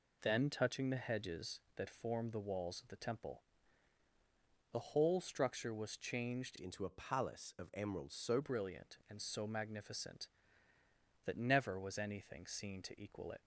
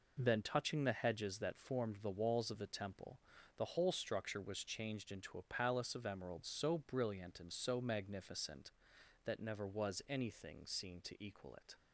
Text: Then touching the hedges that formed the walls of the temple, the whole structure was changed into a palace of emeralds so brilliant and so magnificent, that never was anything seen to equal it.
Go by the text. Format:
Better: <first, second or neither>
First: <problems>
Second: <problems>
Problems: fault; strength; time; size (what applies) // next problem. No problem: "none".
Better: second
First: changes voice from "into" to "so"; from 6.5 to 8.3 s; 1.8 s long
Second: none